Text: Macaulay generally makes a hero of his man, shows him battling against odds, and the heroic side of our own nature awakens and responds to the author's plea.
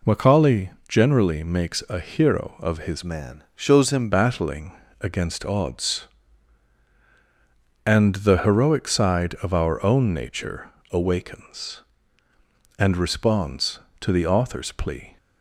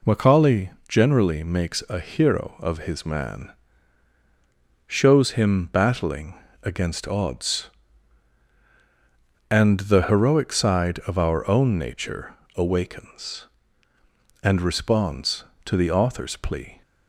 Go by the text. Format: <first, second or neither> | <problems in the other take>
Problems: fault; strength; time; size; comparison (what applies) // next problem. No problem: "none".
second | pauses between "Macaulay" and "generally"; slight; at 0.6 s; 0.20 s long; slight in the second // changes voice from "man" to "him"; from 3.0 to 4.1 s; 1.1 s long // pauses between "battling" and "against"; slight; at 4.7 s; 0.28 s long; slight in the second // pauses between "nature" and "awakens"; slight; at 10.7 s; 0.20 s long; slight in the second